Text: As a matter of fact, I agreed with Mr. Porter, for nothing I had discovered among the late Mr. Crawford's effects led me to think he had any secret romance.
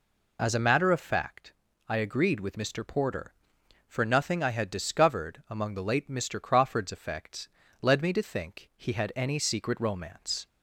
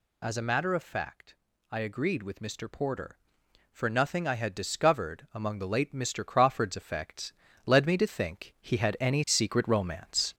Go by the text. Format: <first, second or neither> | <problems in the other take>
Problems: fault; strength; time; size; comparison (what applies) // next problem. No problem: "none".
first | gets louder; noticeable; throughout; 4 dB // pauses between "effects" and "led"; slight; at 7.3 s; 0.32 s long; slight in the first